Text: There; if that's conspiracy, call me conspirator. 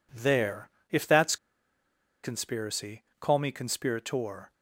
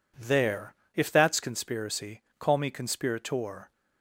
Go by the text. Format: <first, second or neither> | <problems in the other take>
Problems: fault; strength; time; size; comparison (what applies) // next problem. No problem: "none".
second | pauses between "that's" and "conspiracy"; noticeable; at 1.3 s; 0.87 s long